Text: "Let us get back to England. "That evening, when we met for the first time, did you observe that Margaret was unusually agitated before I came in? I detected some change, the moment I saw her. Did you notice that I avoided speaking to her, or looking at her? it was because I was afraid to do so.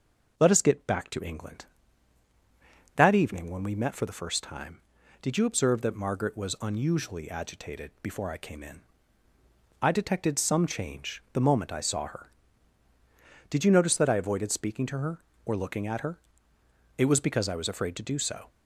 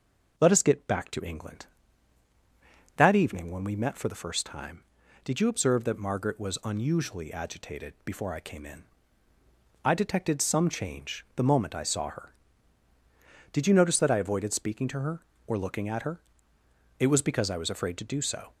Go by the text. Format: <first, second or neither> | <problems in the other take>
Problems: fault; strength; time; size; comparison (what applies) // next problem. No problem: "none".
neither | none